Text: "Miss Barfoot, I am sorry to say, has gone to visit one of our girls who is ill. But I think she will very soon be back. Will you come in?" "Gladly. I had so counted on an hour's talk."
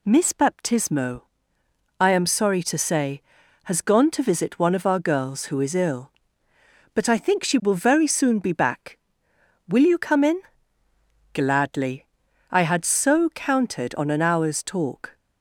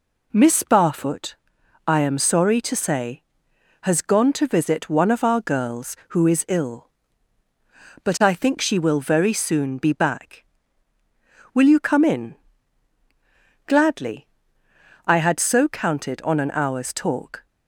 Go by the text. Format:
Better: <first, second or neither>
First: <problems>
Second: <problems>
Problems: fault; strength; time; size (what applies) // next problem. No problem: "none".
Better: second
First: says "Baptismo" for "Barfoot"; at 0.3 s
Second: none